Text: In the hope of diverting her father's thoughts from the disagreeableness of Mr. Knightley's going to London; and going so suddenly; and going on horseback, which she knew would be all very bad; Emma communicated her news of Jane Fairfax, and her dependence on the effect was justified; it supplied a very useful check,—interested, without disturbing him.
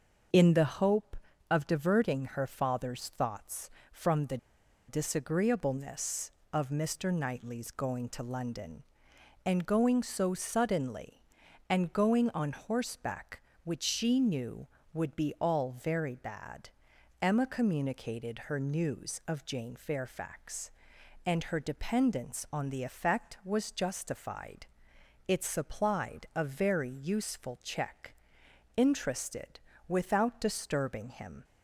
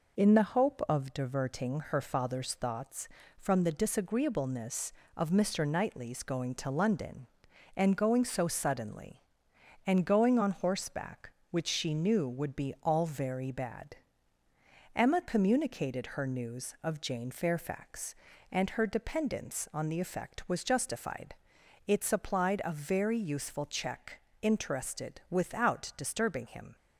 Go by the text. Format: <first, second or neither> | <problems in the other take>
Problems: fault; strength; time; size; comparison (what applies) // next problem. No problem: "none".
second | starts louder than the rest; until 1.6 s; 6.5 dB // pauses between "the" and "disagreeableness"; noticeable; at 4.3 s; 0.51 s long